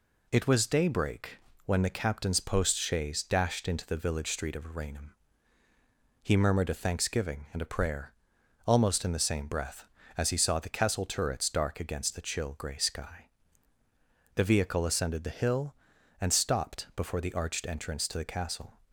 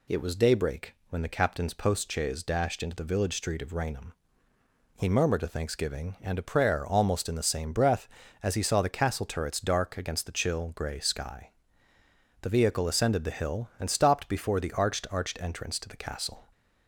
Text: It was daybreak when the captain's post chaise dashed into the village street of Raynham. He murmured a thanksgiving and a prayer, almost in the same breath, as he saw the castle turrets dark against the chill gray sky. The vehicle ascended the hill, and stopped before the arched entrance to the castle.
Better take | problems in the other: first | pauses between "daybreak" and "when"; slight; at 0.9 s; 0.16 s long; slight in the first // says "arched" twice; at 15.1 s

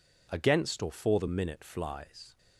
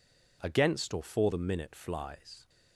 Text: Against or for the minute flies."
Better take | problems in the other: neither | none

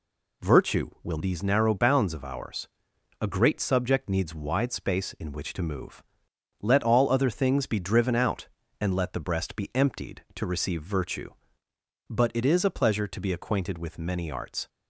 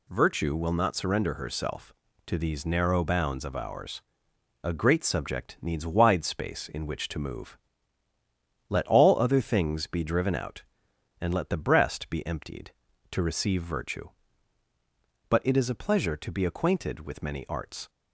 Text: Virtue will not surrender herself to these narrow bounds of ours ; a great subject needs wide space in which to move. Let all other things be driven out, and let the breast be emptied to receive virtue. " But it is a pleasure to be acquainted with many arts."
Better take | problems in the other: second | skips "not surrender herself to"; at 1.1 s

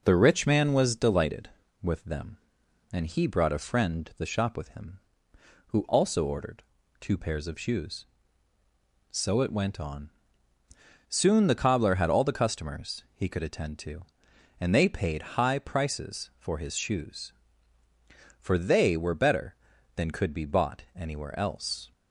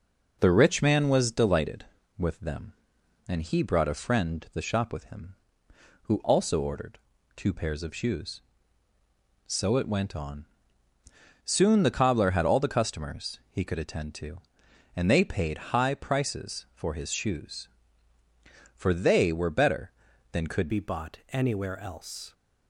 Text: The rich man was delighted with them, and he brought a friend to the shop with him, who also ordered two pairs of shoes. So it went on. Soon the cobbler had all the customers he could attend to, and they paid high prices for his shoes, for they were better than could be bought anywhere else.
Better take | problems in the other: first | pauses between "ordered" and "two"; at 6.9 s; 0.38 s long; also in the first // changes voice at "be"; from 20.6 s on; 1.7 s long

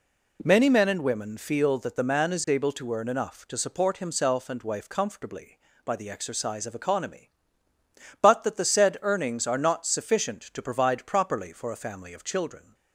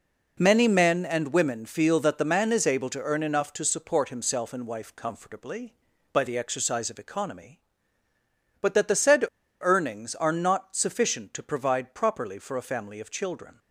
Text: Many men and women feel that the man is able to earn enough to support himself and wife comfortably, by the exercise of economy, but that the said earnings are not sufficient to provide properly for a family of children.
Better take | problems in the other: first | pauses between "said" and "earnings"; at 9.2 s; 0.37 s long

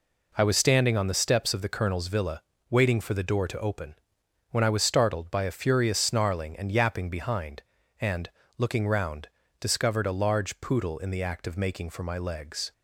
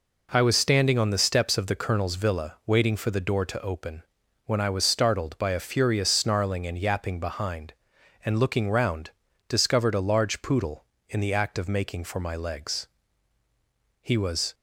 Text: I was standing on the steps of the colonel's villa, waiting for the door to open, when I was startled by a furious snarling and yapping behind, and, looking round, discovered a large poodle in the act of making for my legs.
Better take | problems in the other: first | goes on to say "He was"; from 14.0 s on; 0.52 s long

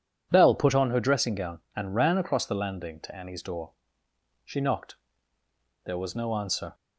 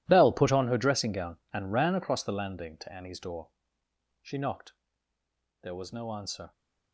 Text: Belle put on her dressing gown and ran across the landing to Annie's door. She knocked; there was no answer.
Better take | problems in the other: first | gets quieter; strong; throughout; 15.5 dB

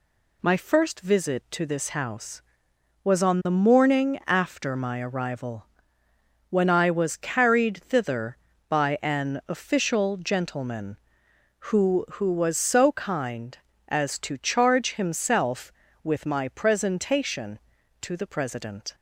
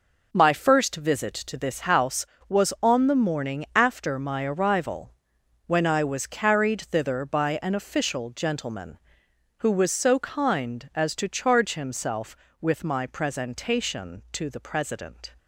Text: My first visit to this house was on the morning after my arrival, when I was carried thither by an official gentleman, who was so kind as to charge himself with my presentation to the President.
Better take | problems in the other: second | says "who" twice; at 12.1 s

